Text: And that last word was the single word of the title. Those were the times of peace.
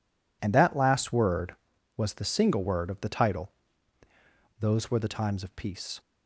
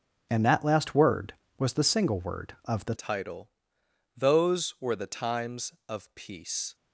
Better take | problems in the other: first | starts louder than the rest; until 1.3 s; 6.5 dB // changes voice at "title"; from 2.9 s on; 3.8 s long

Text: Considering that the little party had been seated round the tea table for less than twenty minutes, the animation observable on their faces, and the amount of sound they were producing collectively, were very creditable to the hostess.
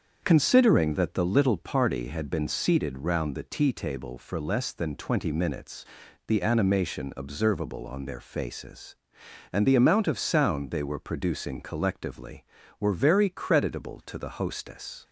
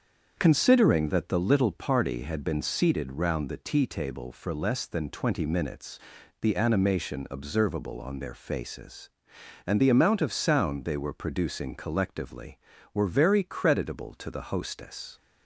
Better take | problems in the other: neither | starts louder than the rest; strong; the same in both

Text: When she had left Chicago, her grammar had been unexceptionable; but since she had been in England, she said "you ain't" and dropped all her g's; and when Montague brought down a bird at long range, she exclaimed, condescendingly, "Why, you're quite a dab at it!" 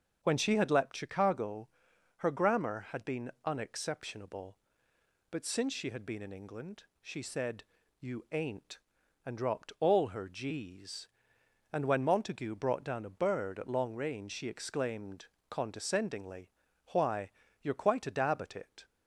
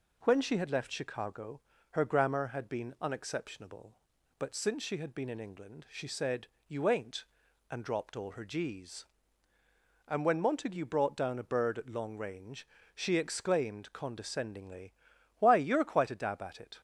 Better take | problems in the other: second | starts louder than the rest; until 1.2 s; 6.5 dB // says "leapt" for "left"; at 0.6 s // pauses between "said" and "you"; slight; at 7.6 s; 0.36 s long; slight in the second

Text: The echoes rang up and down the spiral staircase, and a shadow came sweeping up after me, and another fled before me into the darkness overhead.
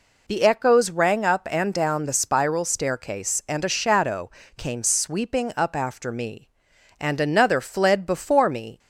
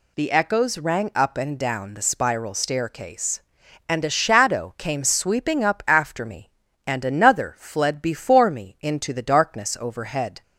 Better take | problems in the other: second | pauses between "shadow" and "came"; slight; at 4.3 s; 0.26 s long // stops before "into the darkness overhead"; at 8.7 s

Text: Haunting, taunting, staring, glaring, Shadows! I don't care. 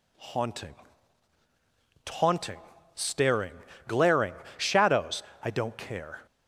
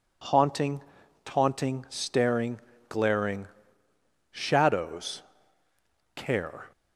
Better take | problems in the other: first | skips "I don't"; at 5.6 s

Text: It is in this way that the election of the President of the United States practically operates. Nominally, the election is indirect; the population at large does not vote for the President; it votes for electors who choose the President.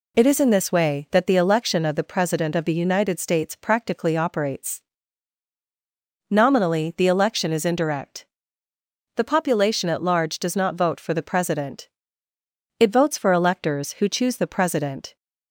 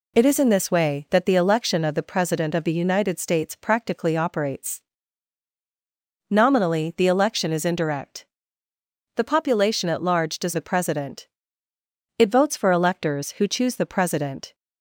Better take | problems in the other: first | skips "not vote for"; at 10.5 s

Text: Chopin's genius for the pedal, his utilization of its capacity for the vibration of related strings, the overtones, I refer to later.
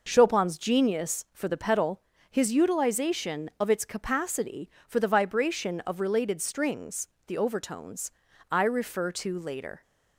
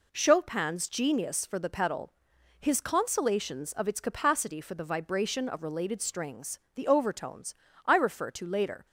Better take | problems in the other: first | says "consolations" for "utilization"; at 2.8 s

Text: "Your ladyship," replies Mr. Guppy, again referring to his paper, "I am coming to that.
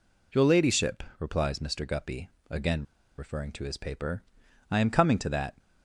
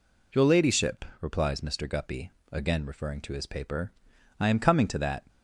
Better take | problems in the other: second | pauses between "again" and "referring"; slight; at 2.8 s; 0.34 s long

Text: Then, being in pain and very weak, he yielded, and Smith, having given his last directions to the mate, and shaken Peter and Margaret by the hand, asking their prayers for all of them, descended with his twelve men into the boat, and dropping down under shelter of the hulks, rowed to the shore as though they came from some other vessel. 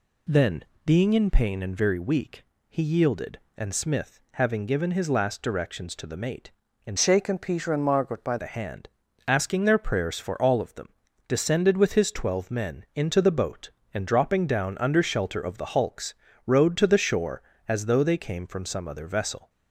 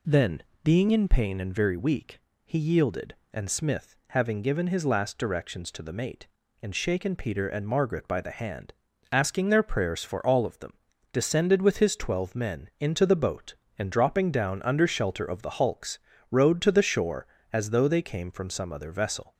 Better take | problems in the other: second | changes voice from "shaken" to "by"; from 6.9 to 8.3 s; 1.4 s long

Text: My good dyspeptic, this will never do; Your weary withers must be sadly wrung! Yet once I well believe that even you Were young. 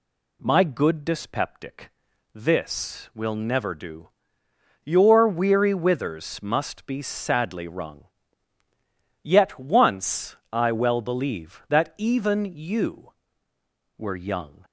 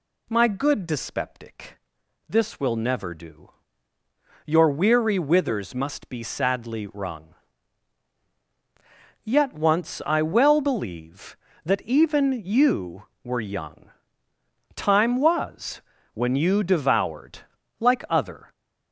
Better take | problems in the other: first | goes on to say "Time was when you devoured like other"; strong; from 14.7 s on; 3.7 s long

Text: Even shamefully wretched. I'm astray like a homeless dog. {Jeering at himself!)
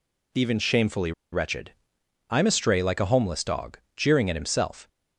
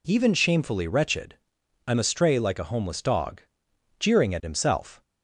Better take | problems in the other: second | pauses between "shamefully" and "wretched"; slight; at 1.1 s; 0.21 s long

